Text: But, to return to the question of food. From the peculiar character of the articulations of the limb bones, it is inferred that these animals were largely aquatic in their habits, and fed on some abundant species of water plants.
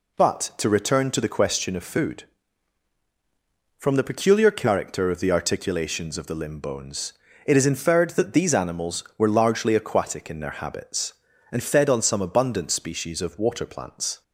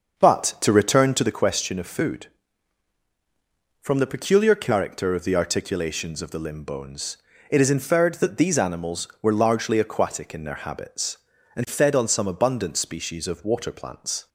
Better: first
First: none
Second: starts louder than the rest; until 1.4 s; 6.5 dB

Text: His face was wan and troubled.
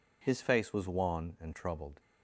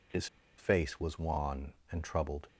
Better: first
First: none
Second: pauses between "His" and "face"; slight; at 0.2 s; 0.32 s long

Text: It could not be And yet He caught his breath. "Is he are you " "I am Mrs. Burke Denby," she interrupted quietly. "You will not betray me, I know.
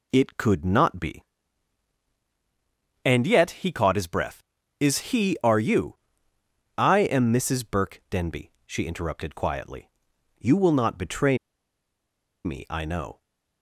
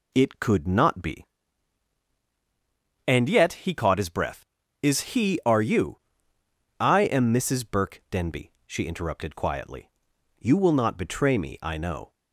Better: second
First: pauses between "betray" and "me"; at 11.3 s; 1.0 s long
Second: none

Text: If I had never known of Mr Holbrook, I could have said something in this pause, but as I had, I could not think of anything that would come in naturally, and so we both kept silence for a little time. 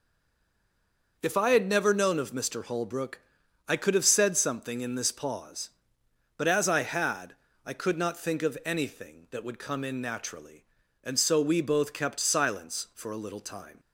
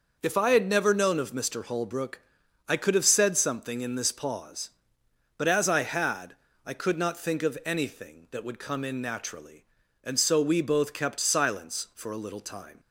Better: second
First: stays silent before the first word; noticeable; until 1.1 s; 1.1 s long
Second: none

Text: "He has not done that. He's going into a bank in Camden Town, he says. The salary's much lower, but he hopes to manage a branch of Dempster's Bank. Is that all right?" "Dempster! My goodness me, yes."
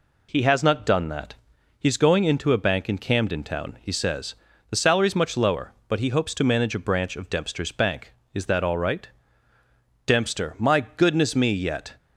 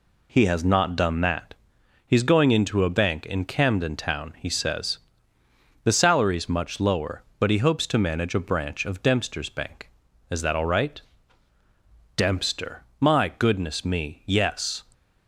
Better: second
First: says "yet" for "yes"; at 11.5 s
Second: none

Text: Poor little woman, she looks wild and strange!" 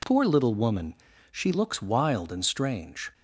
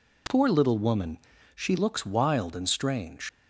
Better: first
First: none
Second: leaves "strange" unfinished; at 3.2 s; 80 ms

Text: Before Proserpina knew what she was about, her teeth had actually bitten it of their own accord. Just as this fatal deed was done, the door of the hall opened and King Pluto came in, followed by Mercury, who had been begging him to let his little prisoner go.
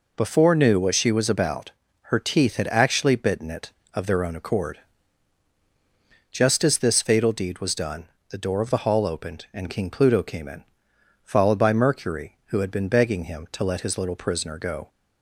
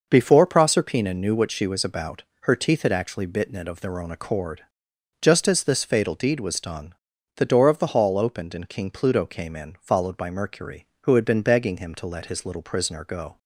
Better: second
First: skips "Proserpina"; at 0.5 s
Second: none

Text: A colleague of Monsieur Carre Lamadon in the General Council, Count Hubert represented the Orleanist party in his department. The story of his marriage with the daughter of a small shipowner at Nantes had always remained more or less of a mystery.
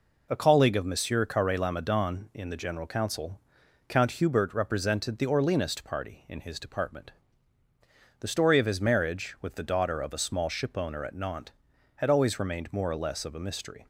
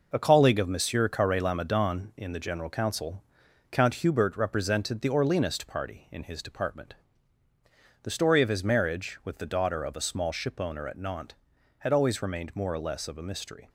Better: first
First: none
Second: gets quieter; throughout; 7 dB

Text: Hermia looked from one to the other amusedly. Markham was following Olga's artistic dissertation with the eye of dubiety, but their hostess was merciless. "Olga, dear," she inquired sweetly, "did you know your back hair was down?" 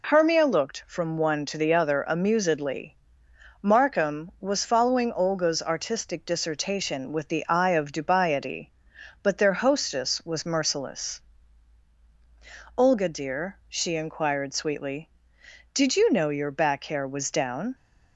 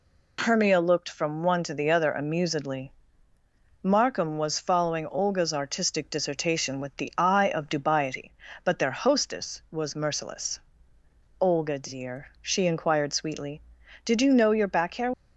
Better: first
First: none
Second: stops before "was down"; at 15.1 s

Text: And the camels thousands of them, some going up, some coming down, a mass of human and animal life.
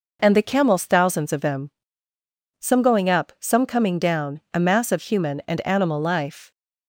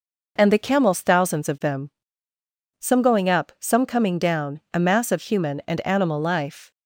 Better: neither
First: none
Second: none

